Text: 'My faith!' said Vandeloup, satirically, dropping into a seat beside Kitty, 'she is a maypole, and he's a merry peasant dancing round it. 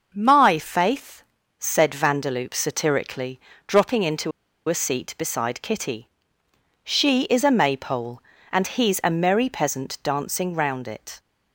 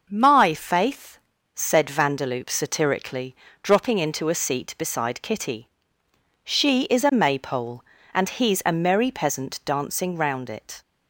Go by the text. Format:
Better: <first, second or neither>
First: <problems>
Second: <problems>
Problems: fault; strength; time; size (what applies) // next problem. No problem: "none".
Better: second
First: pauses between "into" and "a"; at 4.3 s; 0.38 s long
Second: none